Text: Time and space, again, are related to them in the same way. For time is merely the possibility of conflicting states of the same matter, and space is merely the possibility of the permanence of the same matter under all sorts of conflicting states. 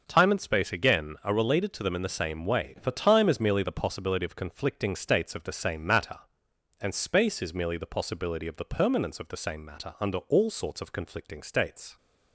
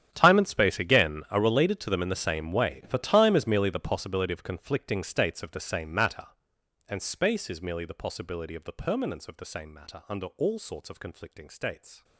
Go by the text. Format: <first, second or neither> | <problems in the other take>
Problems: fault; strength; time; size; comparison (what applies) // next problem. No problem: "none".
first | gets quieter; strong; throughout; 18.5 dB // starts louder than the rest; strong; until 1.1 s; 10 dB; also in the first